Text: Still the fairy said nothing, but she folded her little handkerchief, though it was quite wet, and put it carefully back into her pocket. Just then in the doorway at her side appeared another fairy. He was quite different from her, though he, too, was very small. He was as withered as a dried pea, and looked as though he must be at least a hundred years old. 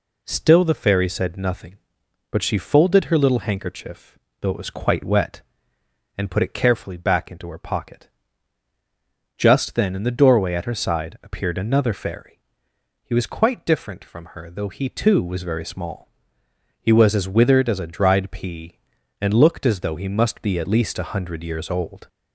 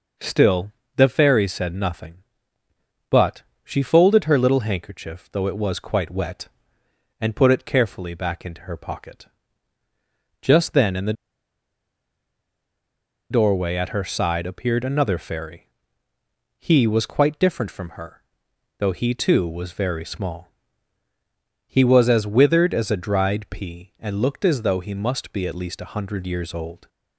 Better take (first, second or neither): first